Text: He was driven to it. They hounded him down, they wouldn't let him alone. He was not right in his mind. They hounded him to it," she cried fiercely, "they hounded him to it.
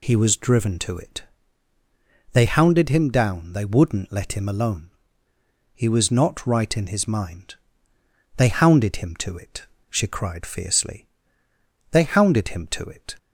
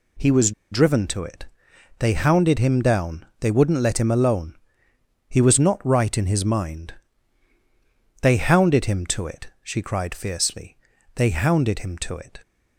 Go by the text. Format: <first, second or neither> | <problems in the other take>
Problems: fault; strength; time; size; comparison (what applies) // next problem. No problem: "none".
first | pauses between "was" and "driven"; slight; at 0.5 s; 0.19 s long